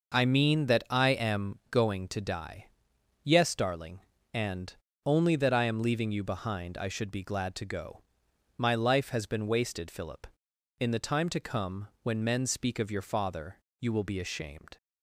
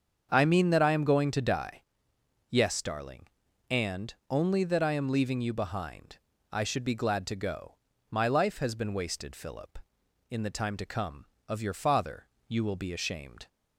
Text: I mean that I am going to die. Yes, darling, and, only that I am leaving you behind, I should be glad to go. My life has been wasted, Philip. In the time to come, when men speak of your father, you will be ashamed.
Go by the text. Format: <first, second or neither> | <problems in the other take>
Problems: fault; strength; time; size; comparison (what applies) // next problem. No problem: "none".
first | starts louder than the rest; strong; until 1.3 s; 7 dB // skips "when men speak"; at 11.3 s